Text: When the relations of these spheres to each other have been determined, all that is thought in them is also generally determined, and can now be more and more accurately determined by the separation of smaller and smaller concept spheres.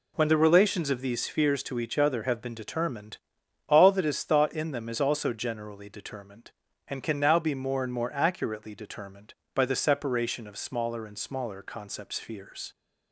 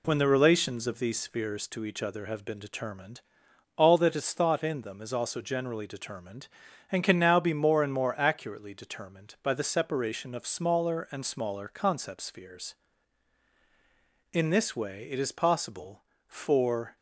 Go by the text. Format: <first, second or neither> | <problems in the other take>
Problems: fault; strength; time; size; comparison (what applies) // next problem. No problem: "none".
first | goes on to say "In this way it is possible for"; strong; from 14.3 s on; 2.6 s long